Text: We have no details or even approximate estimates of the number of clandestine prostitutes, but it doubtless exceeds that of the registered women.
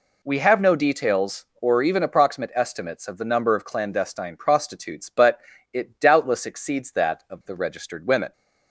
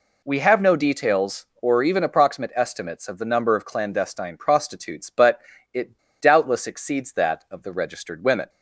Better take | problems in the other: first | pauses between "but" and "it"; slight; at 5.4 s; 0.32 s long; slight in the first // pauses between "it" and "doubtless"; slight; at 5.9 s; 0.21 s long

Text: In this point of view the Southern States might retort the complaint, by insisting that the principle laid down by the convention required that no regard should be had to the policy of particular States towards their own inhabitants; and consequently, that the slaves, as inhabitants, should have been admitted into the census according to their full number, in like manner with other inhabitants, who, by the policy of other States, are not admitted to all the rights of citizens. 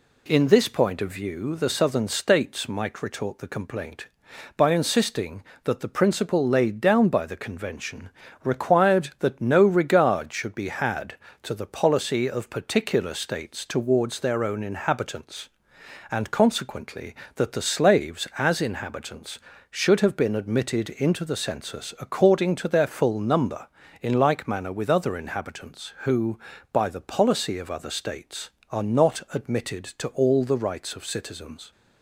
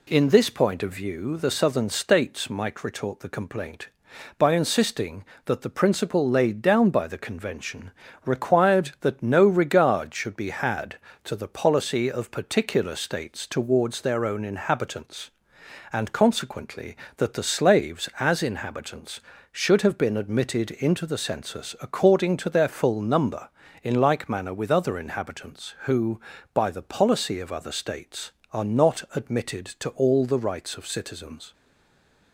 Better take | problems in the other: first | pauses between "convention" and "required"; slight; at 7.9 s; 0.34 s long; slight in the first // stays silent after the last word; slight; from 31.5 s on; 0.8 s long

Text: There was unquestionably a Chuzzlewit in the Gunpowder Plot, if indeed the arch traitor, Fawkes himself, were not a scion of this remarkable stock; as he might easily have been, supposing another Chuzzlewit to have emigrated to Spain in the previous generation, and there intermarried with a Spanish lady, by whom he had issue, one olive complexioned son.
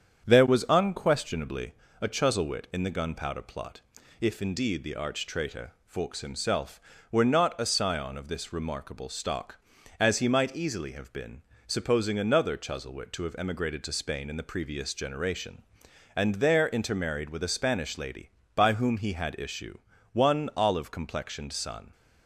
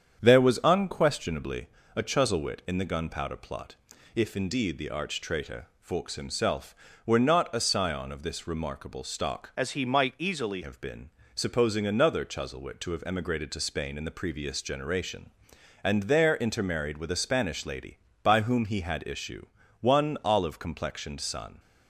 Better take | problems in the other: first | starts louder than the rest; strong; until 1.2 s; 8 dB; strong in the first // pauses between "unquestionably" and "a"; slight; at 1.6 s; 0.28 s long; slight in the first // changes voice from "as" to "easily"; from 9.5 to 10.6 s; 1.1 s long

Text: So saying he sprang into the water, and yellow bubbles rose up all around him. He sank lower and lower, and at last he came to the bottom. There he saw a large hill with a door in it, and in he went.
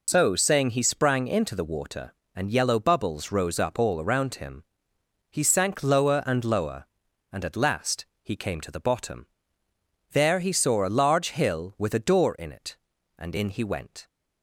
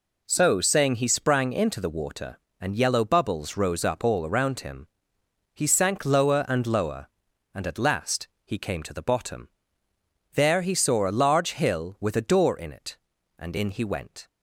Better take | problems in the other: second | loses the start of "So"; at 0.0 s; 70 ms // pauses between "last" and "he"; slight; at 8.0 s; 0.18 s long; slight in the second

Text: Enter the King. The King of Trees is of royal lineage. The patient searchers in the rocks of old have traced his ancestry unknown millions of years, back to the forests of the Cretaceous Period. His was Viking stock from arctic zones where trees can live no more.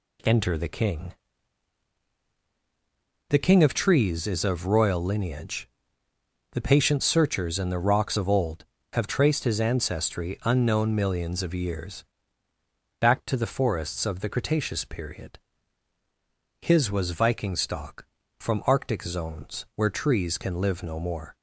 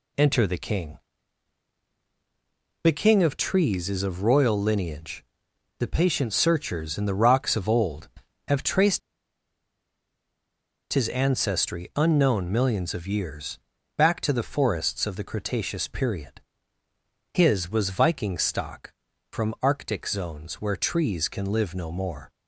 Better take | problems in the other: first | pauses between "traced" and "his"; strong; at 8.9 s; 1.9 s long

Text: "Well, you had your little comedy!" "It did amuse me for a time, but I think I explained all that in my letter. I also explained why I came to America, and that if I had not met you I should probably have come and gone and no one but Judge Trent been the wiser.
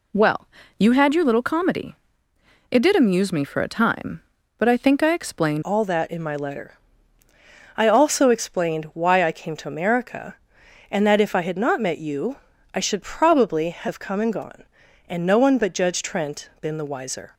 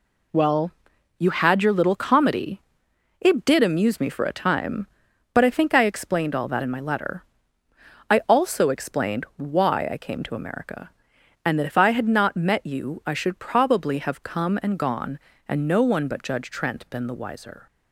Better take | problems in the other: second | changes voice at "all"; from 5.6 s on; 11.7 s long // pauses between "you" and "I"; slight; at 12.3 s; 0.36 s long

